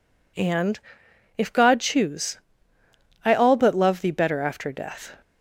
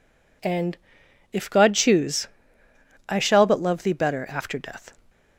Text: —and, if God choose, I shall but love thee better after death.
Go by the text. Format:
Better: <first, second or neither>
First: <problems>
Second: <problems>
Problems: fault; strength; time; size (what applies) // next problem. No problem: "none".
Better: second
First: says "all" for "shall"; at 3.3 s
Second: none